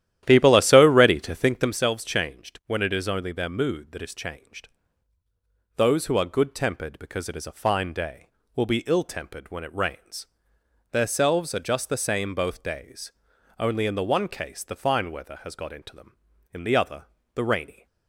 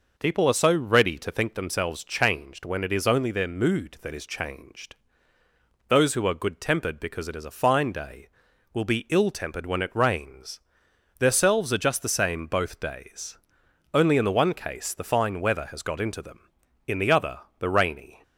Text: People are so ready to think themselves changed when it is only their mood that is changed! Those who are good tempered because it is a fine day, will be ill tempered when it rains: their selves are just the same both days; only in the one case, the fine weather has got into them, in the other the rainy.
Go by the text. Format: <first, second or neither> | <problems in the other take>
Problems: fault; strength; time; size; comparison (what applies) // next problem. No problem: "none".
second | starts louder than the rest; strong; until 1.7 s; 12 dB // pauses between "other" and "the"; slight; at 17.0 s; 0.28 s long; slight in the second